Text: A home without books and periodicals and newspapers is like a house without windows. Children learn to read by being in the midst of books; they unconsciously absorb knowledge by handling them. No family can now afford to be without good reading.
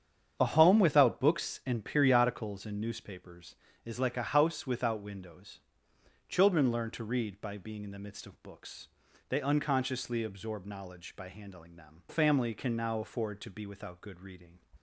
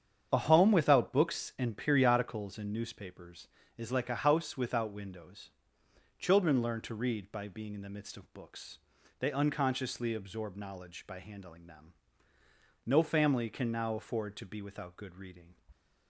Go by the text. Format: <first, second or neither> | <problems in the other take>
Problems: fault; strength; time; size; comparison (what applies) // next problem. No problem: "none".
second | starts louder than the rest; strong; until 1.4 s; 8 dB; strong in the second // skips "No"; at 12.0 s